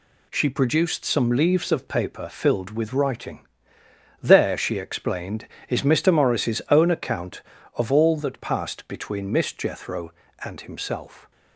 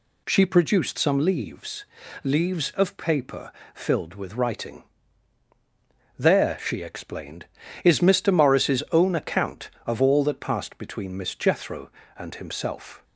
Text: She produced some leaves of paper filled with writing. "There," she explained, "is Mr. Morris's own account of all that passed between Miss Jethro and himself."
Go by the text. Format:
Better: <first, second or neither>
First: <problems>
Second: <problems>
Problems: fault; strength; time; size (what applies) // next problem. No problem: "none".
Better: first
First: none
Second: says "leaves" twice; at 2.2 s // pauses between "paper" and "filled"; slight; at 3.5 s; 0.22 s long